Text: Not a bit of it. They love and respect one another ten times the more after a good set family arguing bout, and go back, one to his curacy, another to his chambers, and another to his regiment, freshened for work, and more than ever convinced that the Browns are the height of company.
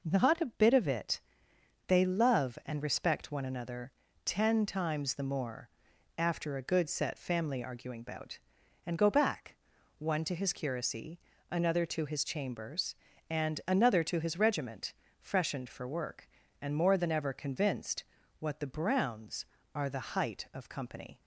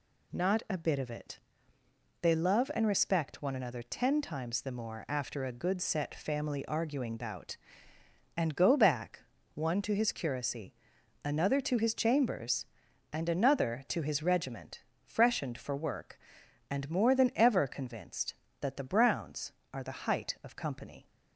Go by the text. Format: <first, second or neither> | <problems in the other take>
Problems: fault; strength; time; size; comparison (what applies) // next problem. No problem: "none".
second | pauses between "another" and "ten"; slight; at 3.9 s; 0.34 s long // pauses between "more" and "after"; noticeable; at 5.6 s; 0.48 s long // says "what" for "that"; at 18.3 s